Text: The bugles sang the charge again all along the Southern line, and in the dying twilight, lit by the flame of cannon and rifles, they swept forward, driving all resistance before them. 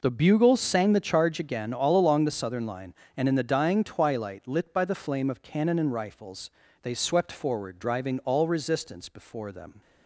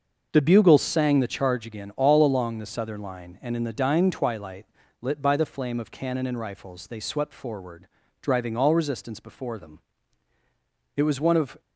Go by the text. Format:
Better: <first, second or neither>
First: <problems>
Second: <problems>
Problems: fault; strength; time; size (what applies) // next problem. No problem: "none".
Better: first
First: none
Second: starts louder than the rest; until 1.3 s; 6 dB // goes on to say "It was one of"; noticeable; from 10.9 s on; 0.68 s long